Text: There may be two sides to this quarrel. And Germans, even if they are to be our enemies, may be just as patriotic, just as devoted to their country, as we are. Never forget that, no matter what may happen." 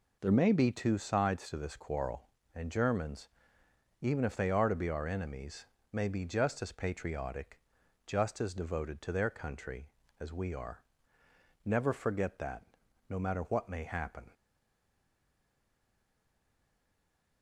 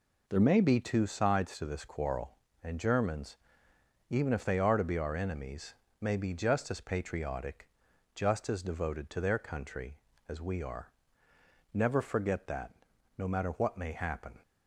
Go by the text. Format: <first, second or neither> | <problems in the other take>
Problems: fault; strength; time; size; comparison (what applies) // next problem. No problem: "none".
second | stays silent after the last word; strong; from 14.3 s on; 3.1 s long